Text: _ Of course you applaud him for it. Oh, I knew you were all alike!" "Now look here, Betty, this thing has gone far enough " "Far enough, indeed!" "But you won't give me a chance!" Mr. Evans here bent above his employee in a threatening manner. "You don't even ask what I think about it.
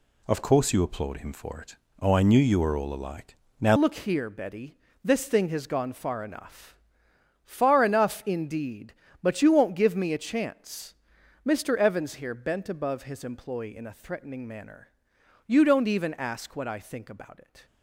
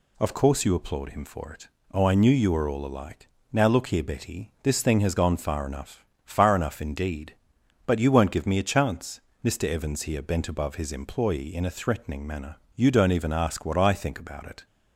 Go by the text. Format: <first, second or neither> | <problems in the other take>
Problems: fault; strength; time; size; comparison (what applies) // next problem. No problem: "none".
second | changes voice at "look"; from 3.7 s on; 13.9 s long